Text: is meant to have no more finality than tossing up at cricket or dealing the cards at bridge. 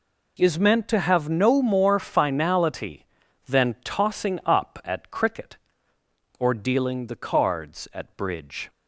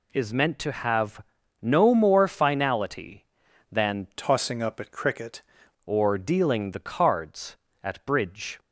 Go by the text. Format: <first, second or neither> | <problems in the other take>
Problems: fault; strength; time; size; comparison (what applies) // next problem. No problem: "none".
first | pauses between "have" and "no"; at 1.2 s; 0.40 s long // changes voice from "tossing" to "cricket"; from 4.1 to 5.4 s; 1.3 s long